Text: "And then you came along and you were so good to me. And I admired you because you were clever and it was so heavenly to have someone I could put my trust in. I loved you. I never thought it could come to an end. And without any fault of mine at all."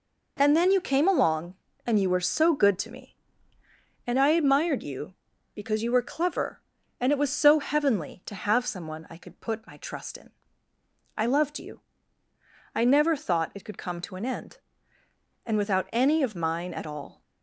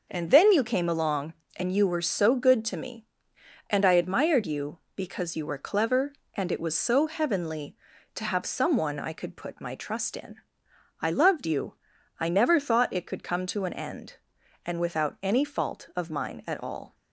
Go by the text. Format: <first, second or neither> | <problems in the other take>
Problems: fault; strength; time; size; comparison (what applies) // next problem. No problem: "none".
second | skips "fault"; at 16.2 s